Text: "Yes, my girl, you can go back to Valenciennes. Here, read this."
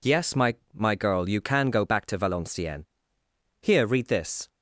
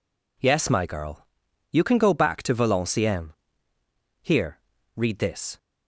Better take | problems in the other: second | says "my" twice; at 0.7 s

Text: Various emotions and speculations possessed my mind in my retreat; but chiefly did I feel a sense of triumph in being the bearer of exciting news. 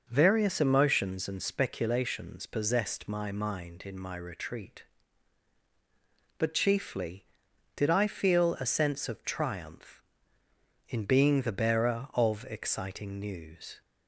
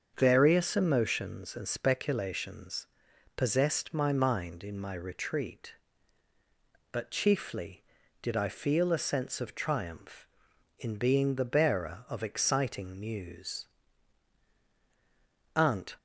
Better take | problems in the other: first | starts louder than the rest; until 1.1 s; 7 dB; noticeable in the first // pauses between "speculations" and "possessed"; noticeable; at 2.8 s; 0.48 s long // goes on to say "Aunt"; slight; from 15.5 s on; 0.40 s long

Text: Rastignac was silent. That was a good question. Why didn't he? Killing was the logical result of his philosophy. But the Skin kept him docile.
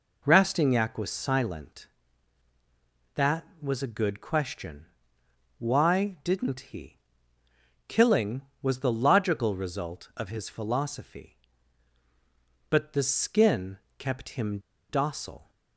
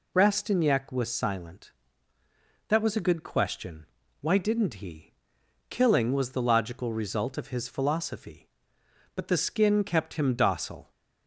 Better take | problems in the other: second | pauses between "Skin" and "kept"; slight; at 13.7 s; 0.20 s long // pauses between "him" and "docile"; slight; at 14.5 s; 0.30 s long

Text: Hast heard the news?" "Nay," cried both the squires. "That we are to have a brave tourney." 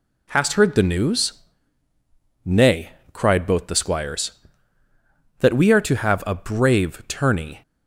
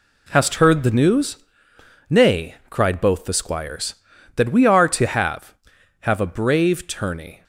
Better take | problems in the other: first | says "have" twice; at 6.0 s

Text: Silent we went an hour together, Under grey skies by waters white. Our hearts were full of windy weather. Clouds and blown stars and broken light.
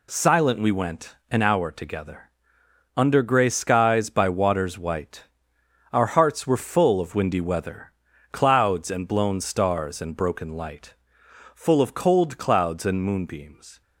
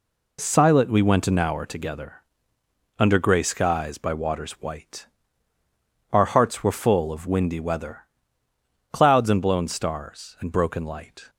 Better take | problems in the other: second | goes on to say "Full of cold clouds and moonbeams"; strong; from 11.5 s on; 2.2 s long

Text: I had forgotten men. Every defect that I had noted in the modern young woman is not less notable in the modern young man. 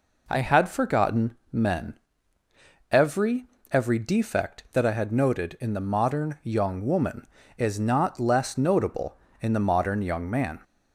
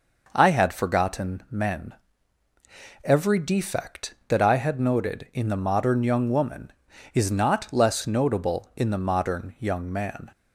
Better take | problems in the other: second | pauses between "forgotten" and "men"; slight; at 1.3 s; 0.16 s long // says "Every" twice; at 3.6 s

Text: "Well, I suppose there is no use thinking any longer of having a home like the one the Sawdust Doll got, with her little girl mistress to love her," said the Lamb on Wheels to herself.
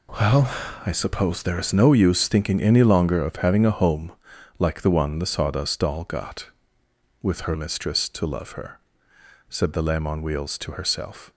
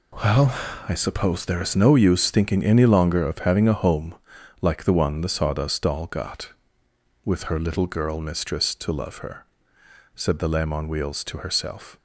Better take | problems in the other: second | pauses between "home" and "like"; noticeable; at 4.1 s; 0.46 s long; noticeable in the second // skips "little girl"; at 7.5 s

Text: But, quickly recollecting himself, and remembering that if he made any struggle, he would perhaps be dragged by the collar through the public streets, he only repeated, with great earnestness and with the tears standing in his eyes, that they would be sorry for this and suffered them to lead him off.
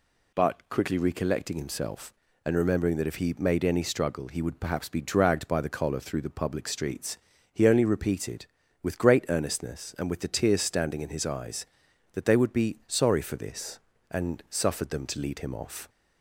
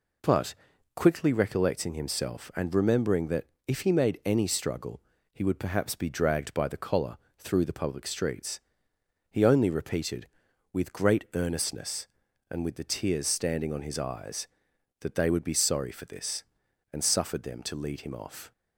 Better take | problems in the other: first | pauses between "that" and "if"; slight; at 3.4 s; 0.20 s long // pauses between "collar" and "through"; slight; at 7.1 s; 0.22 s long // says "on" for "in"; at 13.7 s

